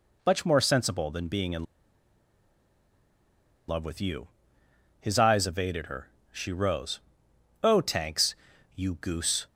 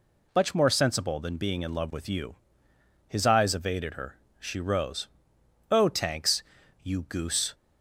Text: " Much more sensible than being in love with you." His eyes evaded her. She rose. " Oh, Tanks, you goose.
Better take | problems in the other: second | pauses between "in" and "love"; strong; at 1.6 s; 2.0 s long

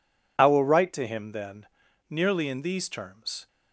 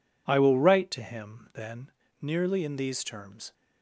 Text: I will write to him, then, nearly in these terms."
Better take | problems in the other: neither | none

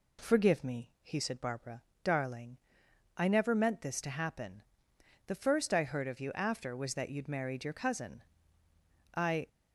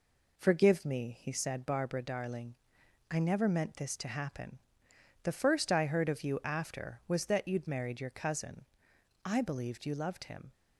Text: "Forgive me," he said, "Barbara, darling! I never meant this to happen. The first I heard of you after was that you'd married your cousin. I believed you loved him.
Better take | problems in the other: second | stops before "believed you loved him"; at 9.4 s

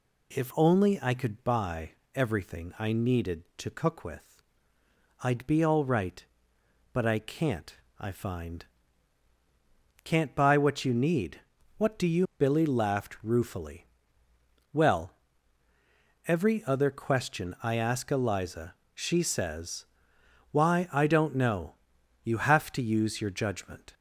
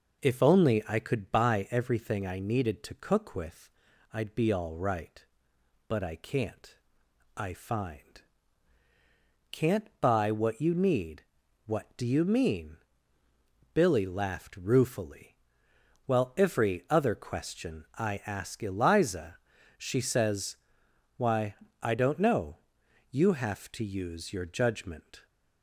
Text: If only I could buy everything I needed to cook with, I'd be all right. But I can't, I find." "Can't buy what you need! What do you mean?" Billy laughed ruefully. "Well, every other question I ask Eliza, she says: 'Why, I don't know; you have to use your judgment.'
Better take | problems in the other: second | pauses between "buy" and "everything"; slight; at 1.9 s; 0.24 s long // skips "mean"; at 12.3 s

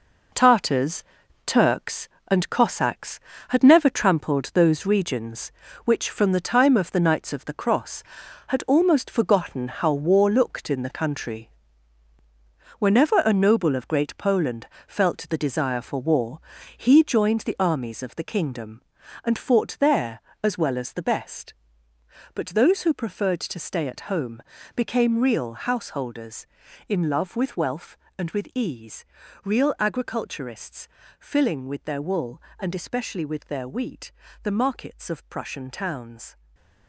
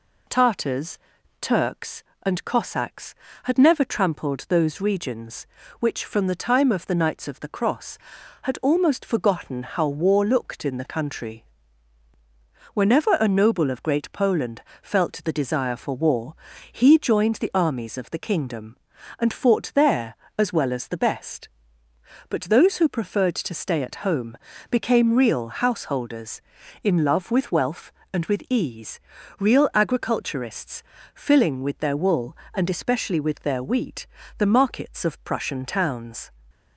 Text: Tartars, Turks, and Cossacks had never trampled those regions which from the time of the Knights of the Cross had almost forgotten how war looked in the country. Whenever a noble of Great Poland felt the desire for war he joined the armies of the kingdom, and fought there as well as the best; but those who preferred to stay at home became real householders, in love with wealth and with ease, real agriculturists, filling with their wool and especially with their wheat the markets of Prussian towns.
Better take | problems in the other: second | gets quieter; strong; throughout; 9 dB // pauses between "Poland" and "felt"; slight; at 14.6 s; 0.20 s long; slight in the second // pauses between "war" and "he"; at 16.3 s; 0.38 s long; also in the second // pauses between "home" and "became"; slight; at 24.4 s; 0.32 s long; slight in the second // pauses between "wheat" and "the"; slight; at 34.1 s; 0.30 s long; slight in the second // stays silent after the last word; slight; from 36.3 s on; 0.5 s long

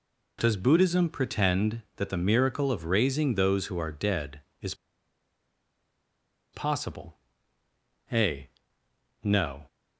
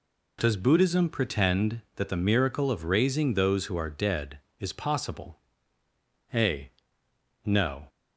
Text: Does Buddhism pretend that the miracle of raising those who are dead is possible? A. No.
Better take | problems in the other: second | pauses between "is" and "possible"; strong; at 4.7 s; 1.7 s long

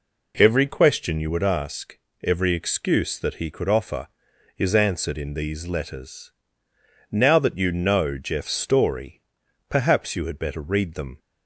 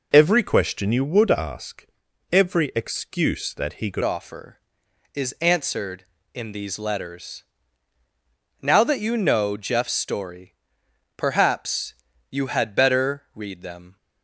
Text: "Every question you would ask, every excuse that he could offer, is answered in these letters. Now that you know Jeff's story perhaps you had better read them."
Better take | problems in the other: first | changes voice at "offer"; from 4.0 s on; 9.9 s long // pauses between "story" and "perhaps"; noticeable; at 10.5 s; 0.64 s long; noticeable in the first // pauses between "perhaps" and "you"; slight; at 11.9 s; 0.36 s long

